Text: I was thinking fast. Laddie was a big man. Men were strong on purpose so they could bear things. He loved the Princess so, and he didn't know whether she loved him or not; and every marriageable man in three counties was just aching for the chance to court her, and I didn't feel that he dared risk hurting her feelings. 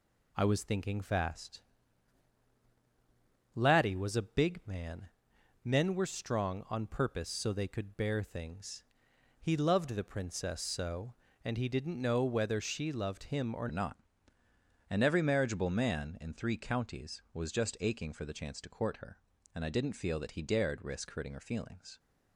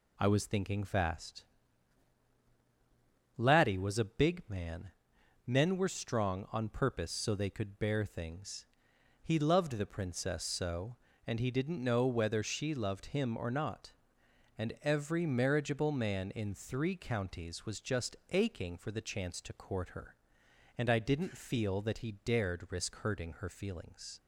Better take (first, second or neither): second